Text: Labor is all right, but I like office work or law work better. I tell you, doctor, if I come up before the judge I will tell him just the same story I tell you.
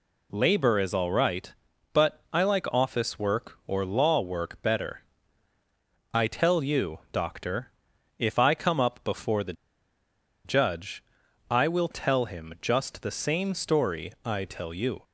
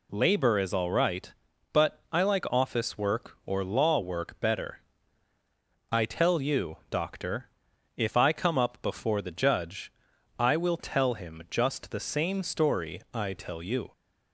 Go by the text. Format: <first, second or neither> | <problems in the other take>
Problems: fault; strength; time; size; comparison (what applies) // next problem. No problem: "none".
second | pauses between "the" and "judge"; noticeable; at 9.5 s; 0.91 s long // pauses between "judge" and "I"; noticeable; at 11.0 s; 0.48 s long; noticeable in the second